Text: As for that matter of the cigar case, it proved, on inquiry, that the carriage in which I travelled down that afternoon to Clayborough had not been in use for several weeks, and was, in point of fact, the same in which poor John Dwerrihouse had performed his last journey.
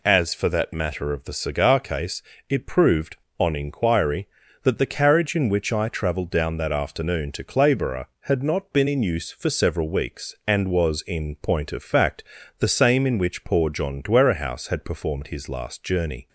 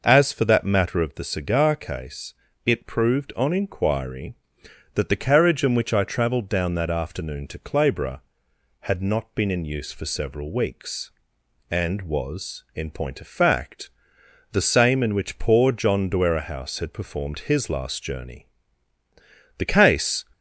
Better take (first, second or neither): first